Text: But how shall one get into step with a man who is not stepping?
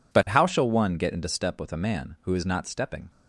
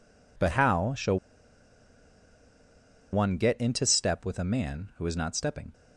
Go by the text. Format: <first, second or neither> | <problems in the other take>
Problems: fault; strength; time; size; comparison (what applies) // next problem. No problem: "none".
first | pauses between "shall" and "one"; strong; at 1.1 s; 1.9 s long